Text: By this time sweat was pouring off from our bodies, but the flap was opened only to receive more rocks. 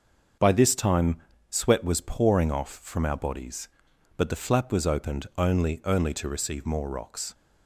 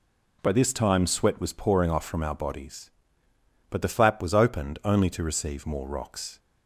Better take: second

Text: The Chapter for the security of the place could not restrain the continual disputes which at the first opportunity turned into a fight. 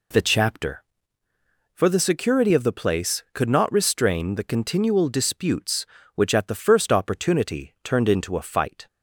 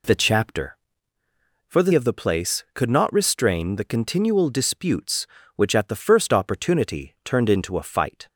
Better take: first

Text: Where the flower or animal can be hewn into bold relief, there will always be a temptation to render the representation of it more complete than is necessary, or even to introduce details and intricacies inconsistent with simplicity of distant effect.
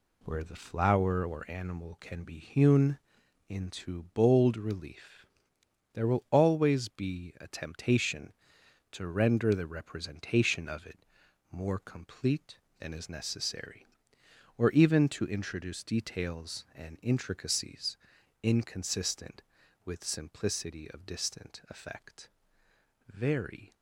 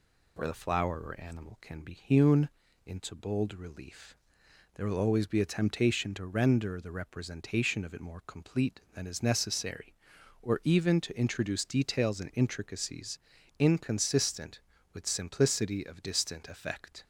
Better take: second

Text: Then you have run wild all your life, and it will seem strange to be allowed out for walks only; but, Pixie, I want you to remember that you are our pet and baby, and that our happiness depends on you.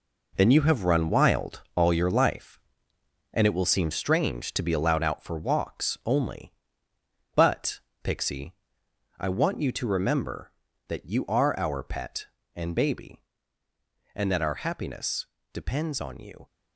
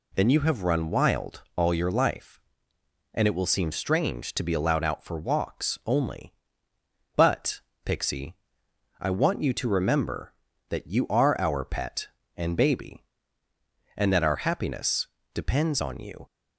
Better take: second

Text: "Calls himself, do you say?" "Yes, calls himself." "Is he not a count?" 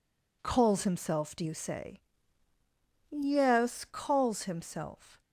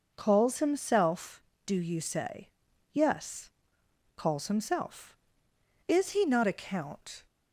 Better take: second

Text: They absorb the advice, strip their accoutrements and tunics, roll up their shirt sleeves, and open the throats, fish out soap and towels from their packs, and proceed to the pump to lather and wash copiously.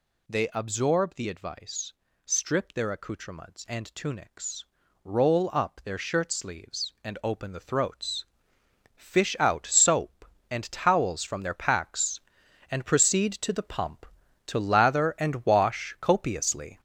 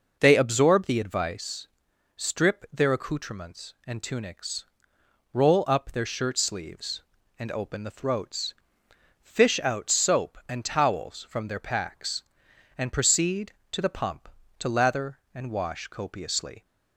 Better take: second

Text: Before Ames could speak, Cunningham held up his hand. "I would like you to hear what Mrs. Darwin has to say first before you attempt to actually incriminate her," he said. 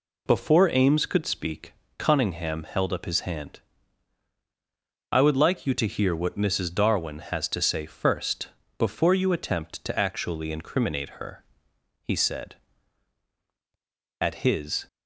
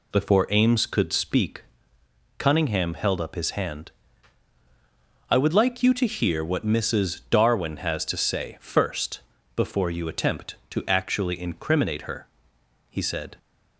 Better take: second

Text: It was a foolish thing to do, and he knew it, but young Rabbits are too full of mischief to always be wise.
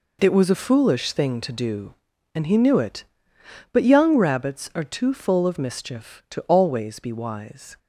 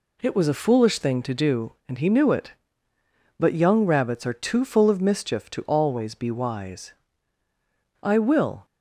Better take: first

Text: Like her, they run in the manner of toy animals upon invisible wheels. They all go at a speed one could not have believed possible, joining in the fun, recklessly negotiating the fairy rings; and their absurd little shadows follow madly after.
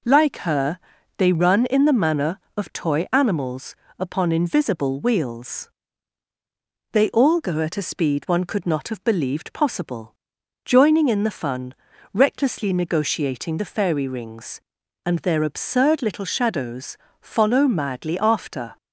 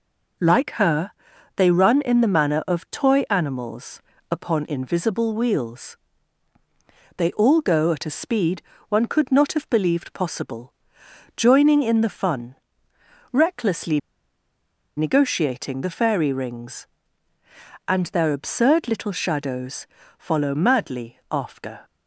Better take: first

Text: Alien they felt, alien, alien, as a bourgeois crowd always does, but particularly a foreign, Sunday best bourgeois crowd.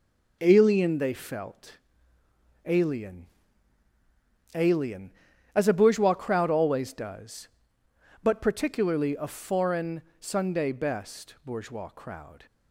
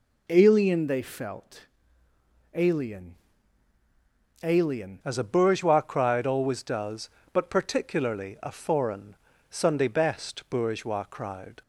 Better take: first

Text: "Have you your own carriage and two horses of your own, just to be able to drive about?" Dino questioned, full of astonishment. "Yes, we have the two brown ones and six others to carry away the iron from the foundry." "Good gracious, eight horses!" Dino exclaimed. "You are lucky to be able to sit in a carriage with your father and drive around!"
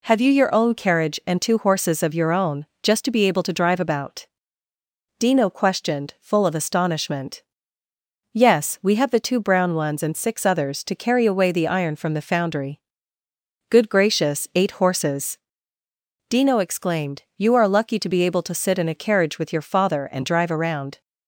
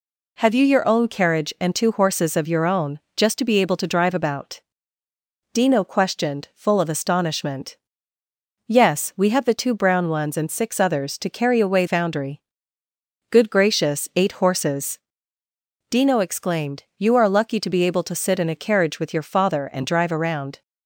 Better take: first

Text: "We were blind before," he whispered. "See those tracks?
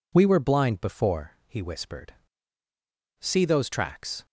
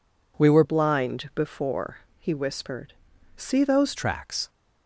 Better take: first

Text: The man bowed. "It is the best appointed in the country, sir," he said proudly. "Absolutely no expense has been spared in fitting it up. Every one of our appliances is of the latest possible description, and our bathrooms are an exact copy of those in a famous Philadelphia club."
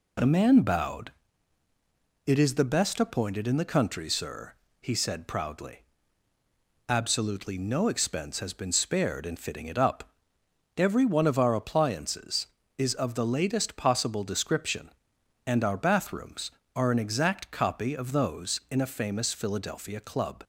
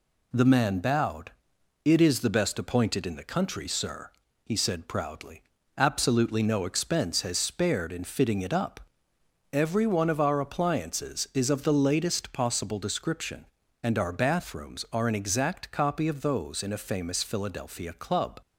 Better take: first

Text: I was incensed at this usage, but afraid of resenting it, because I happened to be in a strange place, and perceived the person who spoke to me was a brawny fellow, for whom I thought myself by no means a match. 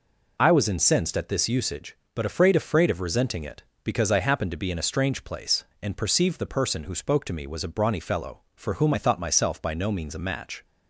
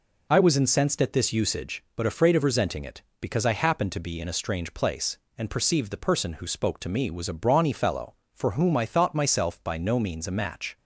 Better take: second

